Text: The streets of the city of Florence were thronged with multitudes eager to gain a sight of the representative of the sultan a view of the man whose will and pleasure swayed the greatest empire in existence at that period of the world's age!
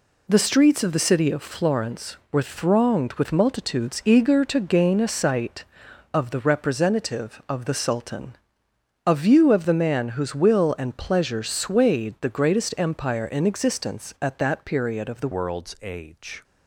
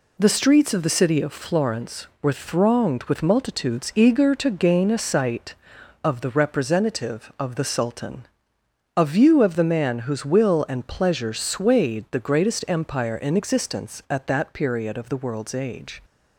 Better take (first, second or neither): second